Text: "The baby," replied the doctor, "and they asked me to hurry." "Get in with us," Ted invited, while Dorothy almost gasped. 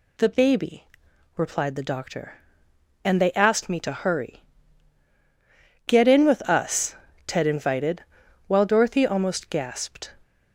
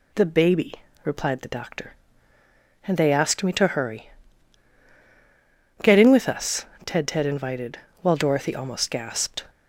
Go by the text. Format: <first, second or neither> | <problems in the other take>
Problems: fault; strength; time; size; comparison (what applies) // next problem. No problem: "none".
first | says "Ted" twice; at 7.0 s